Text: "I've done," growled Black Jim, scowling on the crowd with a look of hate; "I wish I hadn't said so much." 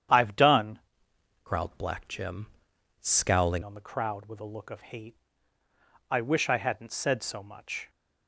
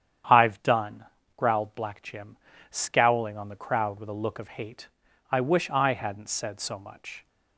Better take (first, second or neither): second